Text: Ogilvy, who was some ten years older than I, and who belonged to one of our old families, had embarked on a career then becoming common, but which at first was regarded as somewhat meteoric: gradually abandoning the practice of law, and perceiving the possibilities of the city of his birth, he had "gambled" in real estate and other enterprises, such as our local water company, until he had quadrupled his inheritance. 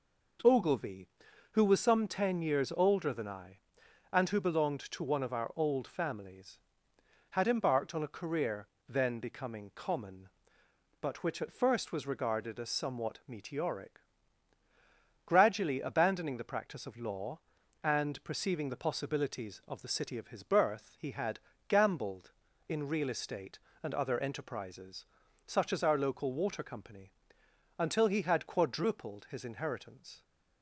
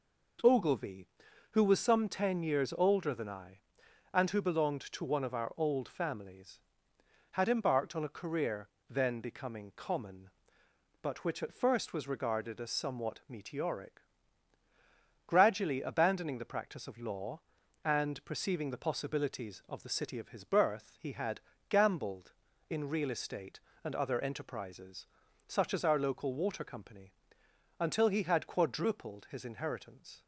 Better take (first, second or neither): neither